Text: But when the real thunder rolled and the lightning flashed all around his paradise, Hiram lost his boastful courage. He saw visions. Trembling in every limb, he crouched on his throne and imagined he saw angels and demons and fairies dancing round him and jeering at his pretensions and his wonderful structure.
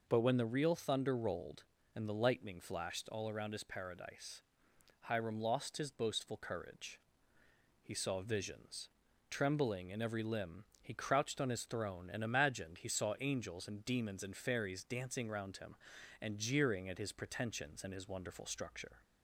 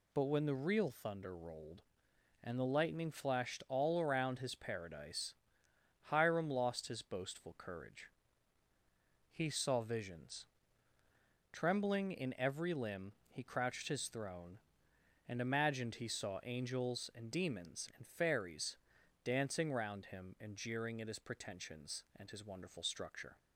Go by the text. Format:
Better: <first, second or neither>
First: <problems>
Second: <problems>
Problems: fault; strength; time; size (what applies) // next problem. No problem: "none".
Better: first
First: none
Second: skips "on"; at 13.8 s // pauses between "fairies" and "dancing"; noticeable; at 18.7 s; 0.48 s long